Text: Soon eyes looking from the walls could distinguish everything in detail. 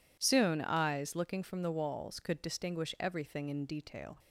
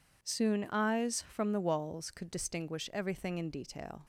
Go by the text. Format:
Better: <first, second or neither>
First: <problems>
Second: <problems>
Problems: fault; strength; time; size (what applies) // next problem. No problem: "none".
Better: first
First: none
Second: skips "looking"; at 1.2 s